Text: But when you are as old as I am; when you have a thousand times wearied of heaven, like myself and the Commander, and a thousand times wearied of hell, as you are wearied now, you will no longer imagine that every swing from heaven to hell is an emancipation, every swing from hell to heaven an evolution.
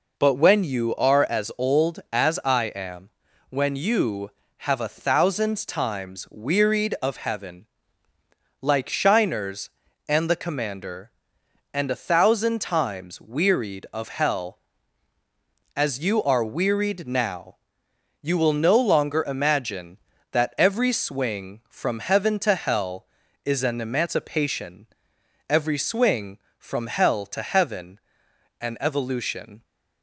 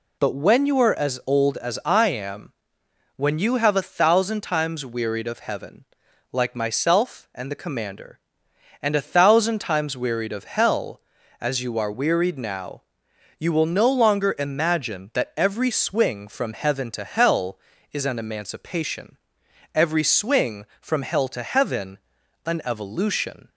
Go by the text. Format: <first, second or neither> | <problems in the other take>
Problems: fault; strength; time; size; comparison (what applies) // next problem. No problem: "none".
second | says "shiners" for "myself"; at 8.8 s // pauses between "heaven" and "an"; noticeable; at 27.9 s; 0.62 s long; noticeable in the second